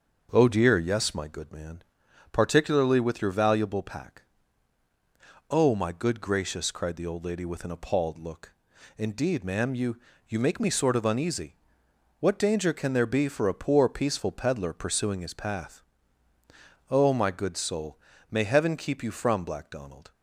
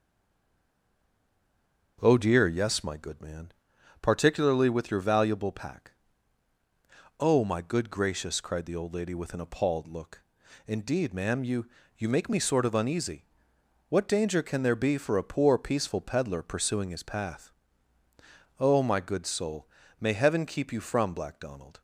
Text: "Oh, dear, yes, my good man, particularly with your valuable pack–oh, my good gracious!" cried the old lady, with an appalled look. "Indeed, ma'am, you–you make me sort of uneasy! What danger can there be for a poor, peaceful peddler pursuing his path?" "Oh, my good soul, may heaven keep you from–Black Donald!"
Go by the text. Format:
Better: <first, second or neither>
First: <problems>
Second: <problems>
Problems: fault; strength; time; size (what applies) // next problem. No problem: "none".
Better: first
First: starts louder than the rest; until 1.3 s; 6.5 dB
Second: stays silent before the first word; noticeable; until 1.9 s; 1.9 s long // starts louder than the rest; until 3.0 s; 6.5 dB